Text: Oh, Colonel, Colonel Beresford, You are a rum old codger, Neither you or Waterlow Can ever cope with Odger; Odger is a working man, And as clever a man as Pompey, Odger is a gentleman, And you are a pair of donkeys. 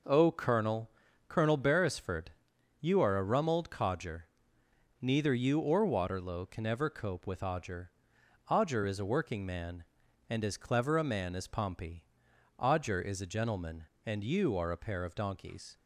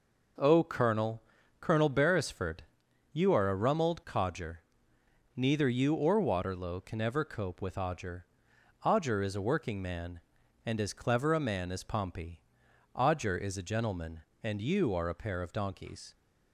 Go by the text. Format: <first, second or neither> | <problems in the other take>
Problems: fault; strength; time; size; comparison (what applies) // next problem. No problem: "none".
neither | none